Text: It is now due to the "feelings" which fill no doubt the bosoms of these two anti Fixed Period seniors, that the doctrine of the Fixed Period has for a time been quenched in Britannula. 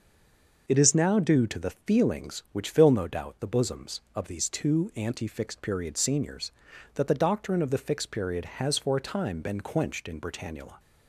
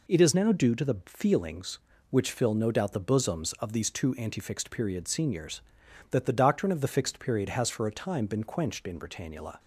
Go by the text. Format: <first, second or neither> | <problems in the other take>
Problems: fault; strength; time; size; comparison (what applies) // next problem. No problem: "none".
second | stays silent before the first word; slight; until 0.6 s; 0.6 s long